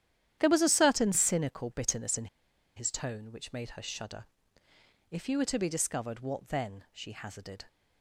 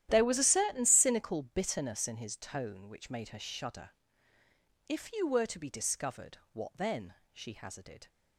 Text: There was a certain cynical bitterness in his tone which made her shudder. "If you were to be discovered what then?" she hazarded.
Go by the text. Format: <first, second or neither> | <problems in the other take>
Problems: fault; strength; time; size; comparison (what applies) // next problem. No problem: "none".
second | starts louder than the rest; strong; until 1.4 s; 11 dB; strong in the second // pauses between "in" and "his"; noticeable; at 2.2 s; 0.50 s long